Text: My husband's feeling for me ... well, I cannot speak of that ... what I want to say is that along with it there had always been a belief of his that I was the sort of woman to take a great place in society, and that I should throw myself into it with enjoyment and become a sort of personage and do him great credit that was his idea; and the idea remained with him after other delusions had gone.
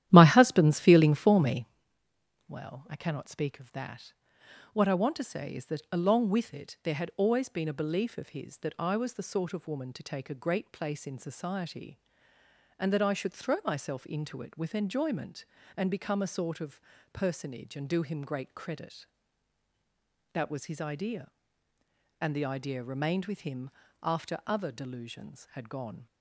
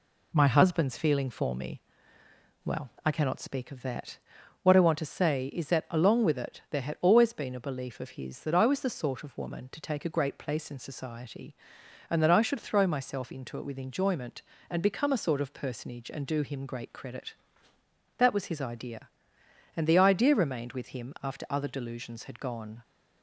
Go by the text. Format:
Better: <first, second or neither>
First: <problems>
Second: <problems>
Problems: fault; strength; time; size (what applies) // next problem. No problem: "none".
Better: second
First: starts louder than the rest; strong; until 1.8 s; 12 dB // pauses between "of" and "personage"; slight; at 16.7 s; 0.32 s long // pauses between "him" and "after"; slight; at 23.6 s; 0.32 s long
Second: none